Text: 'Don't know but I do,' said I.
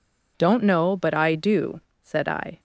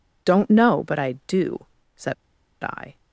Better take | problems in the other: first | pauses between "said" and "I"; noticeable; at 2.1 s; 0.49 s long

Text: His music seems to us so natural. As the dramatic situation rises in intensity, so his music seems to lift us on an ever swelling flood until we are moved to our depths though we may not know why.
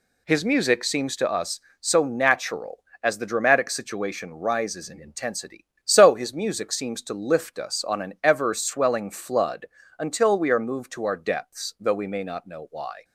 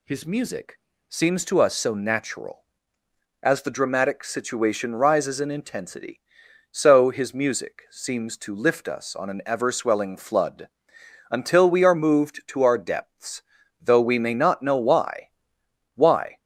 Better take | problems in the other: first | pauses between "music" and "seems"; slight; at 0.7 s; 0.30 s long // pauses between "flood" and "until"; noticeable; at 10.6 s; 0.64 s long; slight in the first // pauses between "depths" and "though"; at 13.4 s; 0.40 s long // says "why" twice; at 15.9 s

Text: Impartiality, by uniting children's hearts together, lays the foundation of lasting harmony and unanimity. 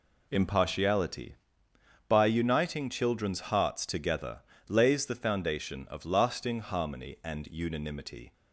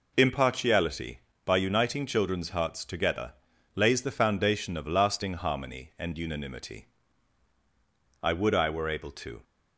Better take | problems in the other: first | goes on to say "I would I were able to"; noticeable; from 8.2 s on; 1.2 s long

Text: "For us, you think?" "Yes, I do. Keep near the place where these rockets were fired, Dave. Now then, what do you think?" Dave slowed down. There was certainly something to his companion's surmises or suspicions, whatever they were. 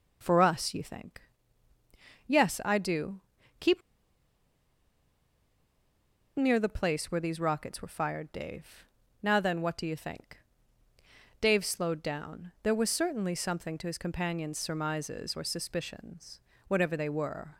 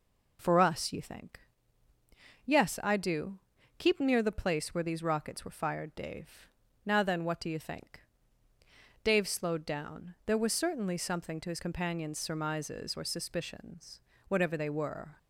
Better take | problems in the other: second | pauses between "Keep" and "near"; strong; at 3.8 s; 2.5 s long

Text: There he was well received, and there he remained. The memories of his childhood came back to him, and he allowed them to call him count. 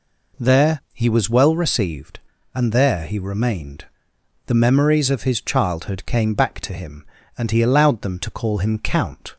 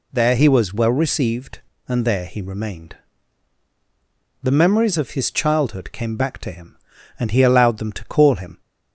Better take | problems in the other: first | stops before "count"; at 8.5 s

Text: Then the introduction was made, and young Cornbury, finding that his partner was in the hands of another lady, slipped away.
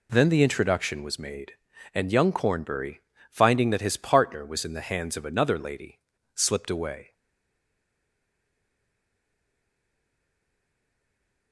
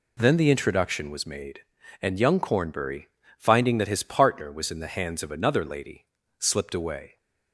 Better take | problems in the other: second | stays silent after the last word; strong; from 7.1 s on; 4.4 s long

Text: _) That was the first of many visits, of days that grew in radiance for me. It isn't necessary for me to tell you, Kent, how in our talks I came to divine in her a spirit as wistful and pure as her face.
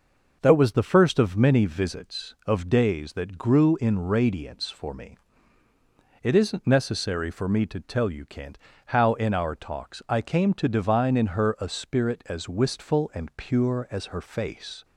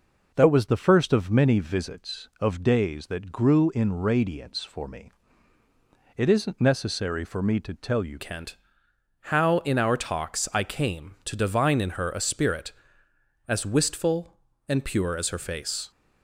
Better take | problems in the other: first | changes voice at "Kent"; from 8.1 s on; 7.8 s long

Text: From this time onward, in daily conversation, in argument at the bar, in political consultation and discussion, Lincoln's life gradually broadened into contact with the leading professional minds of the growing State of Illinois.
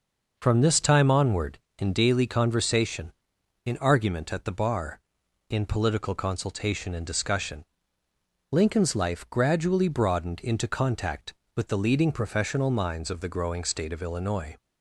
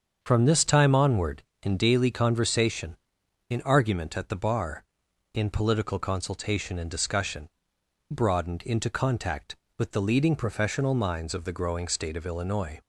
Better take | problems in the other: first | starts louder than the rest; until 1.2 s; 7 dB // skips "Lincoln's life gradually"; at 7.7 s

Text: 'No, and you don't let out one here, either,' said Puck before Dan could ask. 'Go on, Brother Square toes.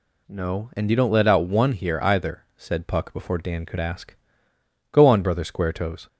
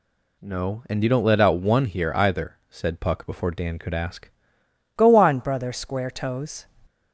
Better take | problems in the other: first | changes voice at "Go"; from 4.9 s on; 1.7 s long

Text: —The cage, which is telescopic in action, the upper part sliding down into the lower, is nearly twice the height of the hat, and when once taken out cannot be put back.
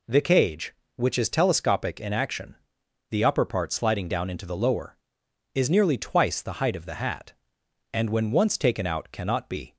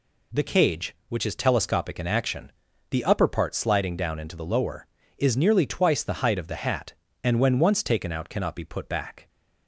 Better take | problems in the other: second | stops before "put back"; at 9.7 s

